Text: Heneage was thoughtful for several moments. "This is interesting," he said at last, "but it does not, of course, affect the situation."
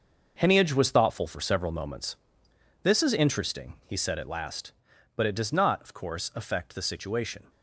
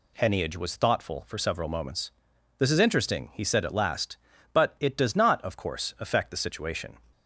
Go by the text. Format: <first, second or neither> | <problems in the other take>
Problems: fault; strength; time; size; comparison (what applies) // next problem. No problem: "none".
second | gets quieter; strong; throughout; 10 dB